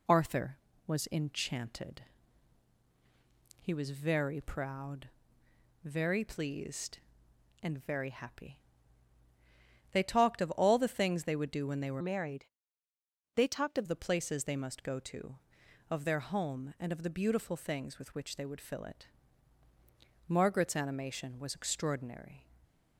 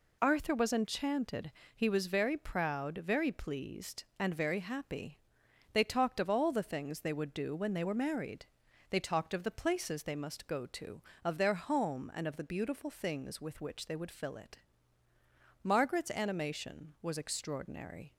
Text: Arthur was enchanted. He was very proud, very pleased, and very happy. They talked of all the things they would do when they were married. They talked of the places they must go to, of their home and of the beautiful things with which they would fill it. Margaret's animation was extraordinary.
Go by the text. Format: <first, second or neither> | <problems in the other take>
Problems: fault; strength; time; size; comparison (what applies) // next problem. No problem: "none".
second | changes voice from "married" to "of"; from 11.9 to 13.8 s; 1.9 s long